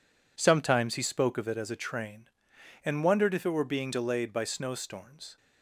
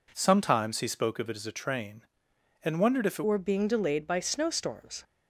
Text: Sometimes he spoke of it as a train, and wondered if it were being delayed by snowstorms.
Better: first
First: none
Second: changes voice at "were"; from 3.2 s on; 1.8 s long

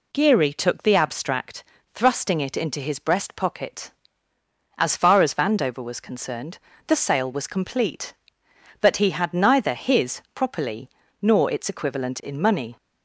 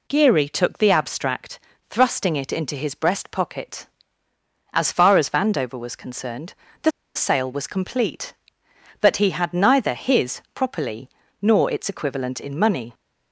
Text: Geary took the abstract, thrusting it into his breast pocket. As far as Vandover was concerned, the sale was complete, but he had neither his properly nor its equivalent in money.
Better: first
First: pauses between "properly" and "nor"; slight; at 10.8 s; 0.32 s long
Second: pauses between "the" and "sale"; slight; at 6.9 s; 0.24 s long // pauses between "properly" and "nor"; slight; at 11.0 s; 0.32 s long

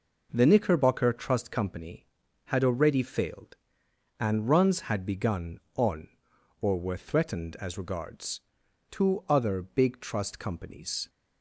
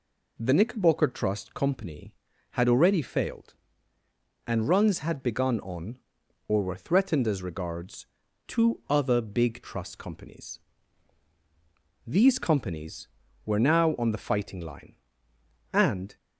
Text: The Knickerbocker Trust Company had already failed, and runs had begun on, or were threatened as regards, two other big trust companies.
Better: first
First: none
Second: goes on to say "These companies were now on the fighting line and"; strong; from 12.0 s on; 4.1 s long

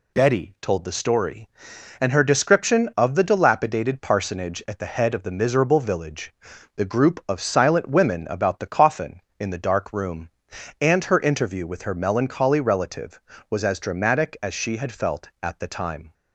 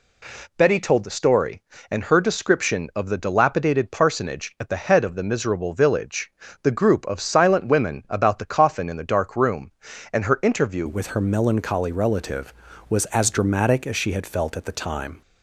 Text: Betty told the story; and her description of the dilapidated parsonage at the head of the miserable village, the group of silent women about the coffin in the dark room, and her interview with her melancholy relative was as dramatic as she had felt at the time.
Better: first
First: none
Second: changes voice at "with"; from 10.8 s on; 4.4 s long

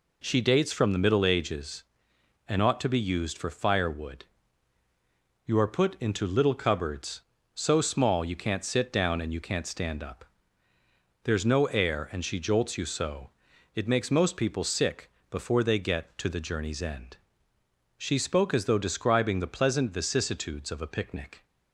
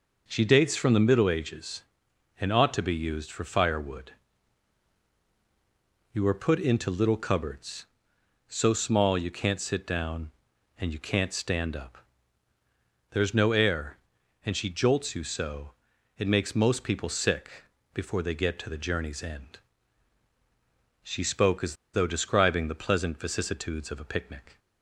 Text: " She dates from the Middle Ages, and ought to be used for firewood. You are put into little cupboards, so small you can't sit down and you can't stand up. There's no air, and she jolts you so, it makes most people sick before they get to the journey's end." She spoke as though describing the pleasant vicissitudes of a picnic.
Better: first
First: pauses between "sick" and "before"; slight; at 15.0 s; 0.22 s long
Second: pauses between "sick" and "before"; slight; at 17.6 s; 0.30 s long // pauses between "as" and "though"; slight; at 21.7 s; 0.18 s long

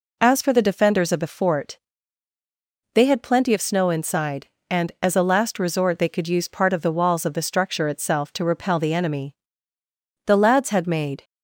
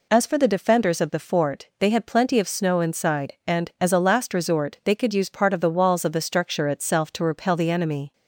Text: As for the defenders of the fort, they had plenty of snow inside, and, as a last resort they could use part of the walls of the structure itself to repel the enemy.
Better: second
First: goes on to say "The lads had made"; noticeable; from 10.2 s on; 0.98 s long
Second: none

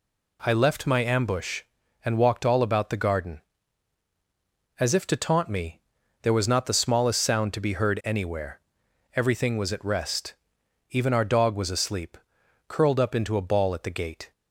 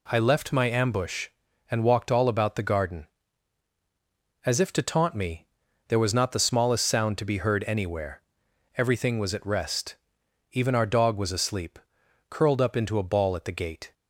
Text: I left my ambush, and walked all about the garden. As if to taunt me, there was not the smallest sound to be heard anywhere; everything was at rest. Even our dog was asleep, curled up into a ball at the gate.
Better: neither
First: none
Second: none

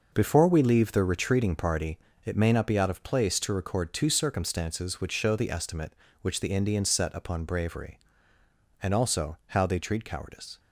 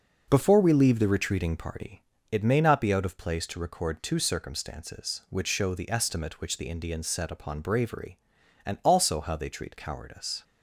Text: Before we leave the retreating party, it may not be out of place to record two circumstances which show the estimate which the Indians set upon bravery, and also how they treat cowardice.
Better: neither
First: none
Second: none

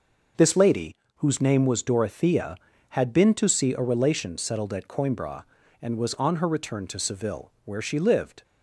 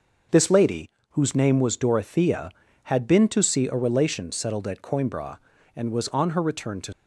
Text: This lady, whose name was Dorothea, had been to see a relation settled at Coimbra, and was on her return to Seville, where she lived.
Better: first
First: none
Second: stops before "Seville where she lived"; at 6.9 s

